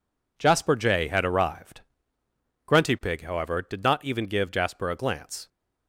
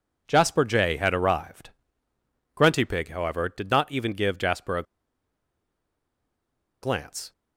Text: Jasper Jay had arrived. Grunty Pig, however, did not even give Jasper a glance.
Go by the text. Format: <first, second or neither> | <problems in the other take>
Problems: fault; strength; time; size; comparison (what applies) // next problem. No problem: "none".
first | pauses between "a" and "glance"; strong; at 4.8 s; 1.9 s long